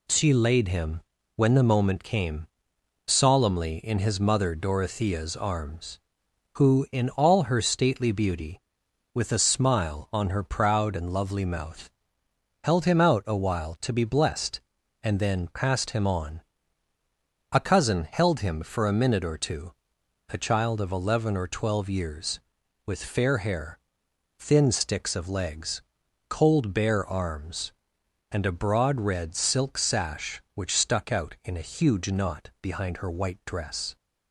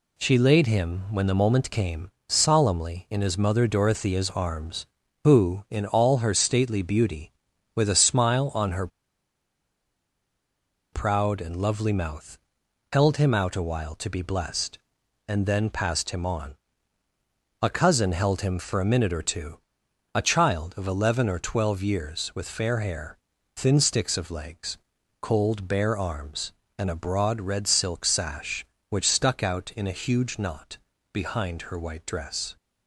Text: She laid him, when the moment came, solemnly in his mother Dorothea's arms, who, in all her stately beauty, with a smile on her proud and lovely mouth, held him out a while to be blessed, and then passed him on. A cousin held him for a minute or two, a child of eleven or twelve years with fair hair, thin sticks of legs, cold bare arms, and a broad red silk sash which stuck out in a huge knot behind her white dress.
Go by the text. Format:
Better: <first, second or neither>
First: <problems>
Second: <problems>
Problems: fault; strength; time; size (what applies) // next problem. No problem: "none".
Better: first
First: none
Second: pauses between "her" and "proud"; strong; at 8.8 s; 2.0 s long // pauses between "knot" and "behind"; slight; at 30.7 s; 0.34 s long